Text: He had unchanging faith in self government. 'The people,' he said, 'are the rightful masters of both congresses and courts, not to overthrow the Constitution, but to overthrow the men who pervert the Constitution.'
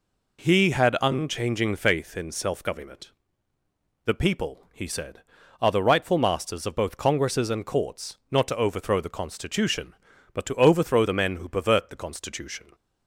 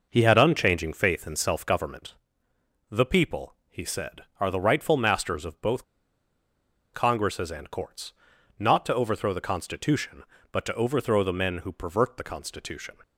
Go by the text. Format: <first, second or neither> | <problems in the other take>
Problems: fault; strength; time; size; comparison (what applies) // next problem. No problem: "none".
first | pauses between "both" and "congresses"; at 5.8 s; 1.0 s long